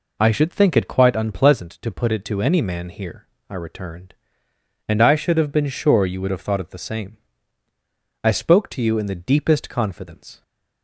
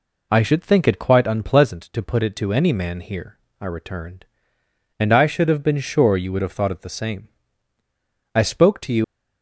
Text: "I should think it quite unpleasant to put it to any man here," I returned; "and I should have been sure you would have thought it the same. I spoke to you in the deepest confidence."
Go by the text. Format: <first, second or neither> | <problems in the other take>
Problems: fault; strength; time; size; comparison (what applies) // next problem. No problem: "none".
first | stops before "in the deepest confidence"; at 9.0 s